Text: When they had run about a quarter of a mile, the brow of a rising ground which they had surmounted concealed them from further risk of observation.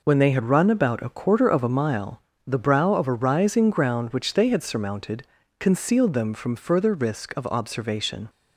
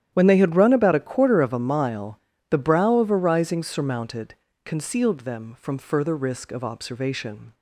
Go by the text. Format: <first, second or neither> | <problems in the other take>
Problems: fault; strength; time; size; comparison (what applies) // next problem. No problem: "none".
first | starts louder than the rest; strong; until 1.1 s; 11 dB // skips "ground which they had"; at 3.6 s // pauses between "surmounted" and "concealed"; slight; at 4.3 s; 0.28 s long; also in the first